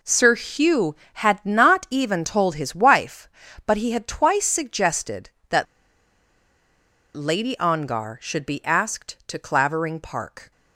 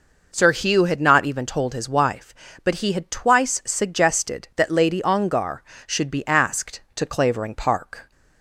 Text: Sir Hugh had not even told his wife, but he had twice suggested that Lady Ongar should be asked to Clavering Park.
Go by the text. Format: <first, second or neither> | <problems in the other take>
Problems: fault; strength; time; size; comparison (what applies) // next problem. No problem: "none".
second | pauses between "that" and "Lady"; strong; at 5.6 s; 1.5 s long